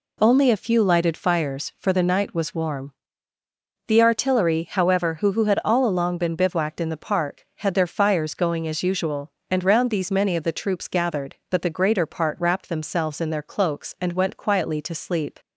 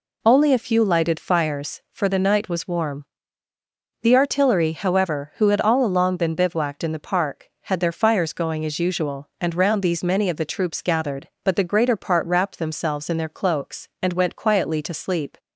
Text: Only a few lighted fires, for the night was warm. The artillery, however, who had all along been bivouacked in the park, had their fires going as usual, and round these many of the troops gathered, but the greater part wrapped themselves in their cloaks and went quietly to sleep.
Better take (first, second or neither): second